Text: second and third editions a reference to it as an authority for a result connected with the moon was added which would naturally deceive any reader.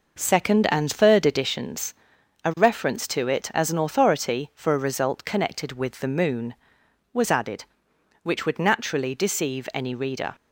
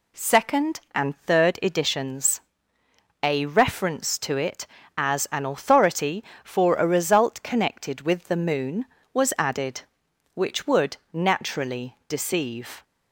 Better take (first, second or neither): first